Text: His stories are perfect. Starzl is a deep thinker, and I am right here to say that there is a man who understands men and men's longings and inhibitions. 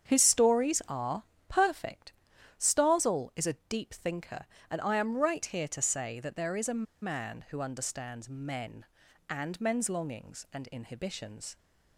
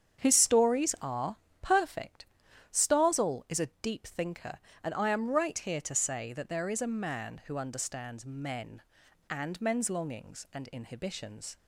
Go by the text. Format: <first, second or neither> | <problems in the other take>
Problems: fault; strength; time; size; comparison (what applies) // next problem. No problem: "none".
second | starts louder than the rest; strong; until 1.1 s; 8 dB; strong in the second // pauses between "are" and "perfect"; slight; at 1.2 s; 0.24 s long; slight in the second // pauses between "a" and "man"; slight; at 6.8 s; 0.19 s long